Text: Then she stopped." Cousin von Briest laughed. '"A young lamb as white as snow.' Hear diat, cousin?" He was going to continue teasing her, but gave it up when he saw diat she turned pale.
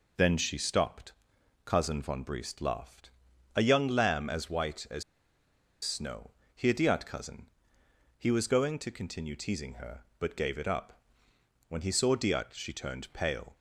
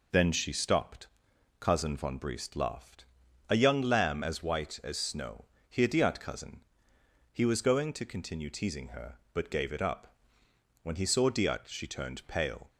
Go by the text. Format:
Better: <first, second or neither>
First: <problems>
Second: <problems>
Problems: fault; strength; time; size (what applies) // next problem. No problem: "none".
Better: second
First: pauses between "as" and "snow"; noticeable; at 5.0 s; 0.80 s long // pauses between "up" and "when"; noticeable; at 11.0 s; 0.66 s long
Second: pauses between "up" and "when"; noticeable; at 10.1 s; 0.66 s long